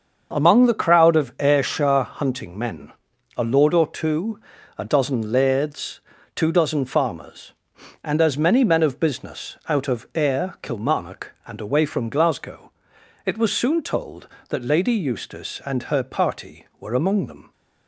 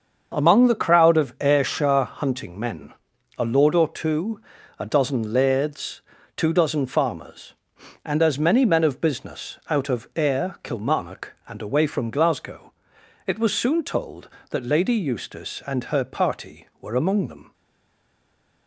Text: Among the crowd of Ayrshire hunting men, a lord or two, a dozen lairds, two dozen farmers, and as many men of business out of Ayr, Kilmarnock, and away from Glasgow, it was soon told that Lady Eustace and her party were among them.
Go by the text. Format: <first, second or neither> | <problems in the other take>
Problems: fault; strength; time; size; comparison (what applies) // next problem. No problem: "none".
first | starts louder than the rest; until 1.3 s; 6.5 dB; also in the first // stays silent after the last word; from 17.5 s on; 1.1 s long